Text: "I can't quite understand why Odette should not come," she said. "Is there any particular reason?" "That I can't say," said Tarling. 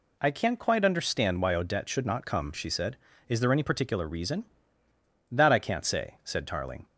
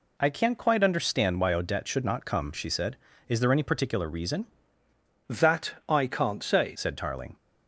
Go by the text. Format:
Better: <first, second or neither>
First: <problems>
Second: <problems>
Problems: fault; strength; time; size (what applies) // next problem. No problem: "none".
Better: first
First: none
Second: changes voice from "That" to "say"; from 5.2 to 6.7 s; 1.5 s long